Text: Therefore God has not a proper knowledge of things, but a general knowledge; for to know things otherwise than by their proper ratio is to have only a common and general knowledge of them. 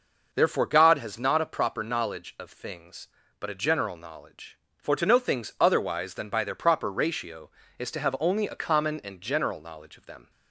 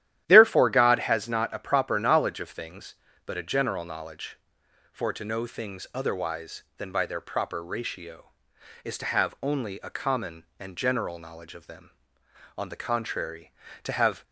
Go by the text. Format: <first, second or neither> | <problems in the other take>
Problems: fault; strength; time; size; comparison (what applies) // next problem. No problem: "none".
first | starts louder than the rest; strong; until 1.2 s; 12 dB // goes on to say "On the contrary To have"; from 12.5 s on; 1.6 s long